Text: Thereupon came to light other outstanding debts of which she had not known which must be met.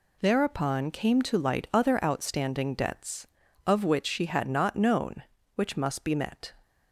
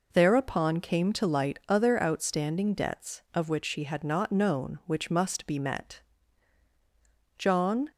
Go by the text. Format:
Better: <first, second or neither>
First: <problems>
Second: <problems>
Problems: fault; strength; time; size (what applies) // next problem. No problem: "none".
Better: first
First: none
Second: goes on to say "John"; from 7.3 s on; 0.52 s long